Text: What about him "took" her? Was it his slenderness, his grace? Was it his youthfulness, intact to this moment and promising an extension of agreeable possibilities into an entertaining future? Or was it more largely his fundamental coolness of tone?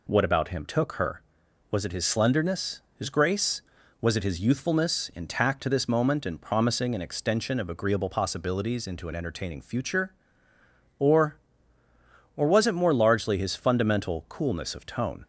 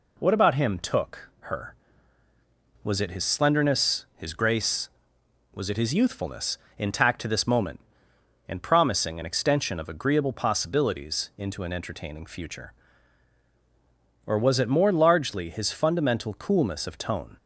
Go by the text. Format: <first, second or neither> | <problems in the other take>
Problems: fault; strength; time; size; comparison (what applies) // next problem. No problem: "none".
second | says "Or" twice; at 12.3 s